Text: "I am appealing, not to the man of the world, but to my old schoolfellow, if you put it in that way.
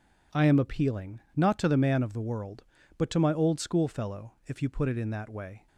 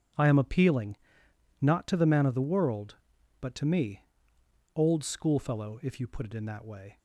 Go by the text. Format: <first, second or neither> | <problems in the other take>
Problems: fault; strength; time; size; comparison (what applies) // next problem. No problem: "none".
first | says "me" for "my"; at 3.6 s